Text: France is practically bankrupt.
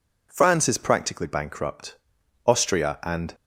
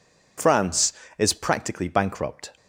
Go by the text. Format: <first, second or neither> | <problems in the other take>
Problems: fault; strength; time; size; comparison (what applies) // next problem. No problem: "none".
second | goes on to say "Austria and"; noticeable; from 2.4 s on; 0.88 s long